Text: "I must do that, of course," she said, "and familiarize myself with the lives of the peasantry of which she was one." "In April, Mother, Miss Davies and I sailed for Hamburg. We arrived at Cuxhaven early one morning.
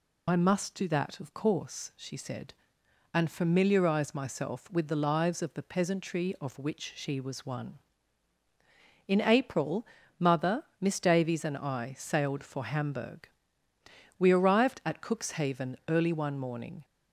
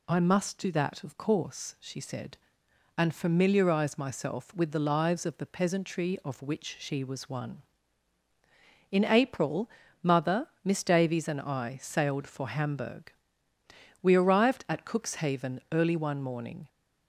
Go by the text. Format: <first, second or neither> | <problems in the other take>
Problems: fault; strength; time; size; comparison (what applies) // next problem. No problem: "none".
second | loses the start of "I"; at 0.2 s; 50 ms